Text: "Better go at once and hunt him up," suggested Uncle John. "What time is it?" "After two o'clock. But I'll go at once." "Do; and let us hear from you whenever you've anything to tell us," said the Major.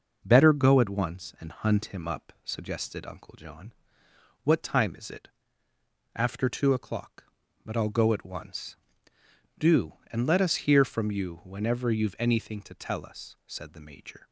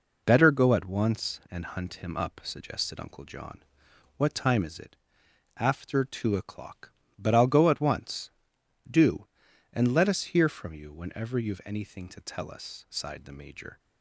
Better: first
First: none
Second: says "sighed" for "said"; at 12.9 s

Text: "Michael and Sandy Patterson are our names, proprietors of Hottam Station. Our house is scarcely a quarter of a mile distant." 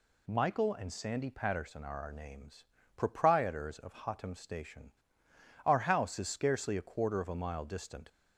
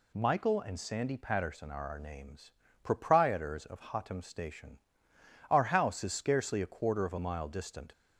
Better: neither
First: none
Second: none

